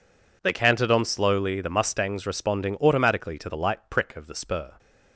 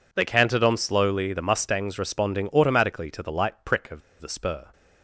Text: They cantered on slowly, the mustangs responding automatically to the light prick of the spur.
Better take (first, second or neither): first